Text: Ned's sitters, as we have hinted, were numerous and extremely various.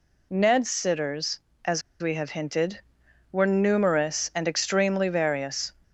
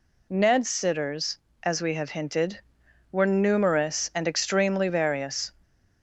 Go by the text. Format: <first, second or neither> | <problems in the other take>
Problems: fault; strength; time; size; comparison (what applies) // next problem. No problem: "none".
second | pauses between "as" and "we"; slight; at 1.8 s; 0.19 s long